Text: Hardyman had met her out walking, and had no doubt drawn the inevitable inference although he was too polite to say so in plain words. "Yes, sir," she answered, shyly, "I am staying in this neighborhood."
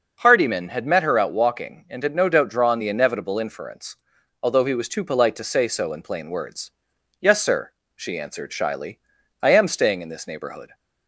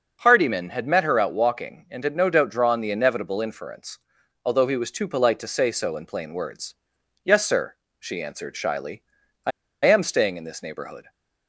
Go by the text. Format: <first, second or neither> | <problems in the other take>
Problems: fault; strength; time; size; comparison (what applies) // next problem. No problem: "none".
first | pauses between "inference" and "although"; noticeable; at 3.9 s; 0.48 s long; noticeable in the first // pauses between "I" and "am"; slight; at 9.5 s; 0.34 s long